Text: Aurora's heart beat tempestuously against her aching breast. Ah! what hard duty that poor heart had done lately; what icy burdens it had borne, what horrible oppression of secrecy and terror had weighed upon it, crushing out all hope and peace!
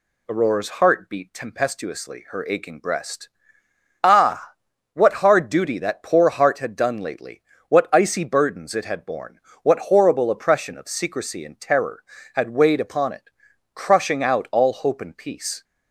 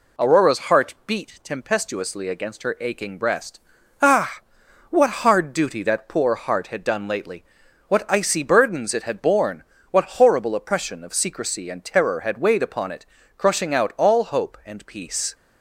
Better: second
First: skips "against"; at 2.2 s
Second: none

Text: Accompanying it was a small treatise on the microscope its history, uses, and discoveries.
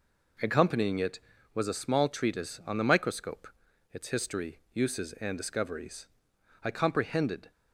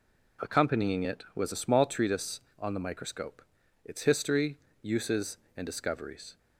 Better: second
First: pauses between "microscope" and "its"; noticeable; at 3.4 s; 0.46 s long // goes on to say "I comprehended"; noticeable; from 6.6 s on; 0.86 s long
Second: pauses between "microscope" and "its"; at 3.4 s; 0.42 s long

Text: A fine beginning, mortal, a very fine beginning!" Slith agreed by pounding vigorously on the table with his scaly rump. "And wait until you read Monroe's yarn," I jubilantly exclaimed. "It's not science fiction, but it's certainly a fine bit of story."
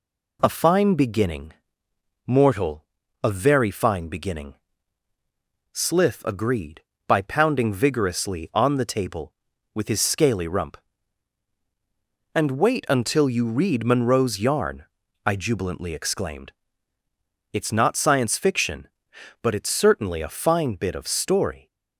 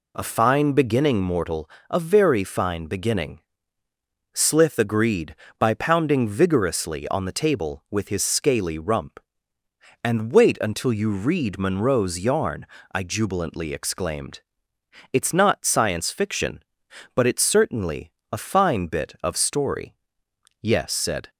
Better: first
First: none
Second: pauses between "certainly" and "a"; slight; at 18.0 s; 0.22 s long // goes on to say "Yes said"; noticeable; from 20.6 s on; 0.68 s long

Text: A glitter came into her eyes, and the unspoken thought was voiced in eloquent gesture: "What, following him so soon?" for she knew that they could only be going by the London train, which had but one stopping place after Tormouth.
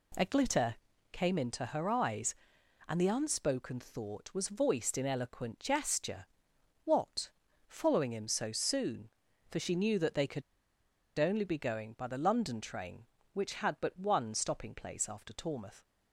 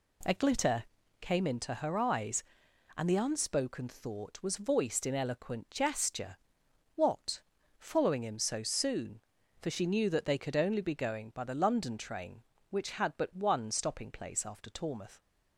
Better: second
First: pauses between "glitter" and "came"; slight; at 0.7 s; 0.36 s long // pauses between "could" and "only"; noticeable; at 10.4 s; 0.77 s long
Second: pauses between "glitter" and "came"; slight; at 0.8 s; 0.36 s long

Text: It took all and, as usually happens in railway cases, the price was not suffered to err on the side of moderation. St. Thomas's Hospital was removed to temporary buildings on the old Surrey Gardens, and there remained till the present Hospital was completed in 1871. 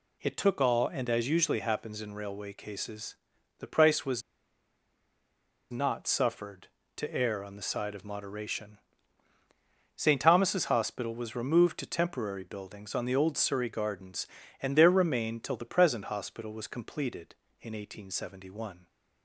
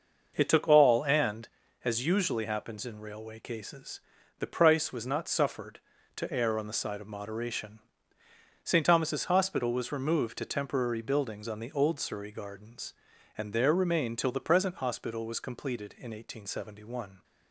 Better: second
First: pauses between "was" and "not"; strong; at 4.2 s; 1.4 s long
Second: none

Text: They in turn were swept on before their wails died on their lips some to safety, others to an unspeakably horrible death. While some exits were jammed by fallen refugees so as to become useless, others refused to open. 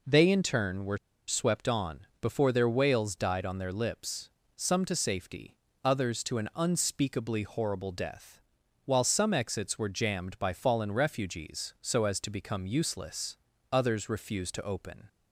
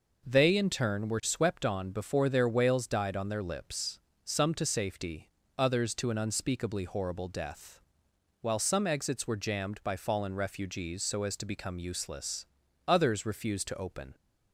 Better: second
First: pauses between "were" and "swept"; slight; at 0.9 s; 0.29 s long // pauses between "on" and "before"; slight; at 2.0 s; 0.16 s long // pauses between "lips" and "some"; slight; at 4.2 s; 0.26 s long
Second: pauses between "lips" and "some"; slight; at 3.9 s; 0.30 s long

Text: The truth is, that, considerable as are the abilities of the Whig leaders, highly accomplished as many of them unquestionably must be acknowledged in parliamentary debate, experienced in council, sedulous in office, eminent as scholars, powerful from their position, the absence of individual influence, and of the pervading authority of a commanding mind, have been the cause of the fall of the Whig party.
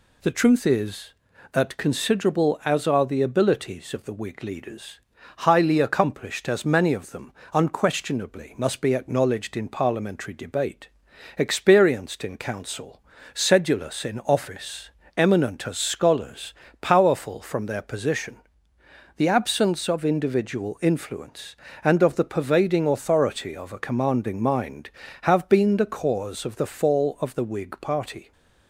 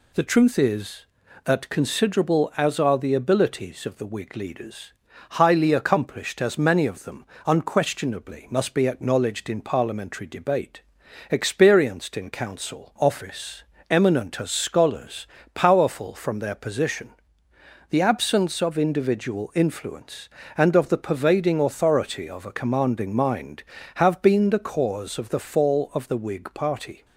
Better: first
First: pauses between "them" and "unquestionably"; slight; at 7.3 s; 0.22 s long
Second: pauses between "them" and "unquestionably"; slight; at 7.2 s; 0.22 s long // skips "sedulous in"; at 12.9 s

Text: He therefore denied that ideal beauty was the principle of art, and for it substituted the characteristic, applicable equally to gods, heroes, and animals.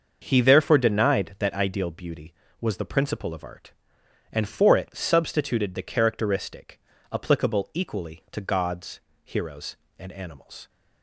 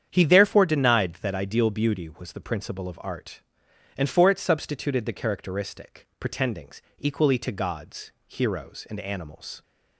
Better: first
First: starts louder than the rest; until 1.2 s; 6.5 dB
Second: starts louder than the rest; strong; until 1.1 s; 8.5 dB // says "pretendings" for "applicable"; at 6.1 s

